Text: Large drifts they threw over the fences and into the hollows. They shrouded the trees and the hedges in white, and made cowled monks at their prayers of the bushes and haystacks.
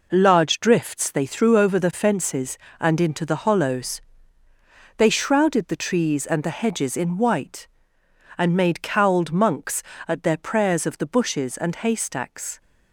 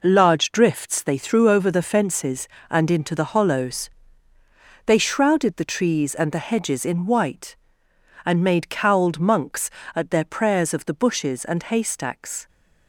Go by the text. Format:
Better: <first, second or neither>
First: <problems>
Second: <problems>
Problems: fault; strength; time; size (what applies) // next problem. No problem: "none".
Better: neither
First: none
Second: none